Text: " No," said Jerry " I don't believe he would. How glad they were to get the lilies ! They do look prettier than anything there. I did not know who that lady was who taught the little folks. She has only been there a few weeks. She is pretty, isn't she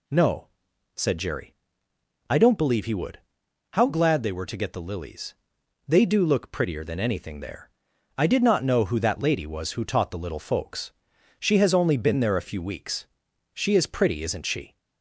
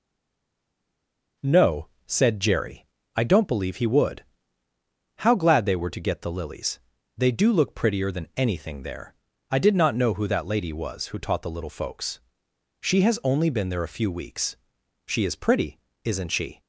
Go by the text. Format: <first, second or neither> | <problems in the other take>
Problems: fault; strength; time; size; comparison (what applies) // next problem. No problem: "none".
first | stays silent before the first word; noticeable; until 1.3 s; 1.3 s long